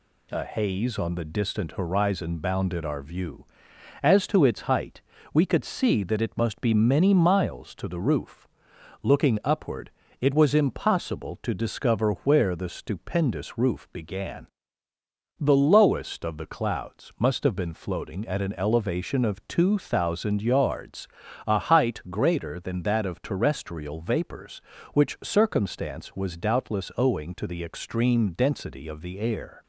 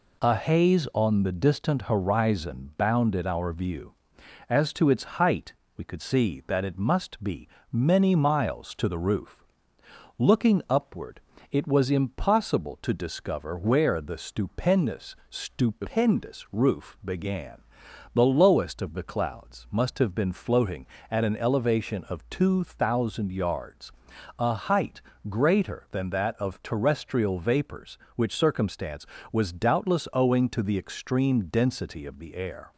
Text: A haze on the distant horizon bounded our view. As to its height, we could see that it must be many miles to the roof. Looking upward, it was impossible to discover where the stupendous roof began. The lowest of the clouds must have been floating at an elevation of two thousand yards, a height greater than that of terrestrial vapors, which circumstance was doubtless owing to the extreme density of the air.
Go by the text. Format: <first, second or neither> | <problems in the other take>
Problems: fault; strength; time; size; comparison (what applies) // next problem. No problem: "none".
first | pauses between "be" and "many"; slight; at 7.4 s; 0.22 s long // says "stupendous" twice; at 15.2 s // pauses between "height" and "greater"; slight; at 25.0 s; 0.26 s long